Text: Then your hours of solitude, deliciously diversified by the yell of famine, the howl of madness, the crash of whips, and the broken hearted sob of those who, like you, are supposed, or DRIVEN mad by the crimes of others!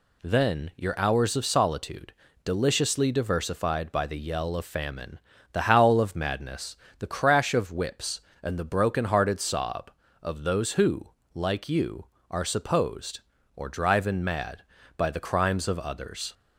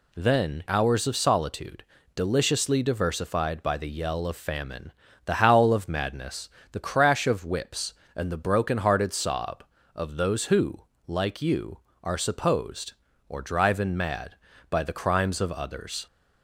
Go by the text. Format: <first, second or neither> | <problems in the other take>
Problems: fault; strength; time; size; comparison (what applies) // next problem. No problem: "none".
first | skips "your"; at 0.6 s